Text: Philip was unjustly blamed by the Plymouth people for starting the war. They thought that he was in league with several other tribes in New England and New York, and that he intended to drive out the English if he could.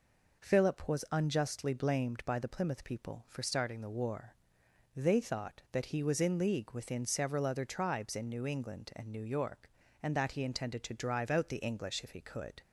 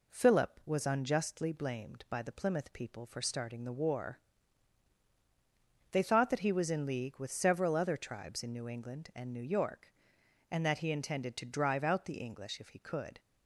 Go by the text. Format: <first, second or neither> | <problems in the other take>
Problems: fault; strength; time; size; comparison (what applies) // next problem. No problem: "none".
second | says "within" for "with"; at 6.7 s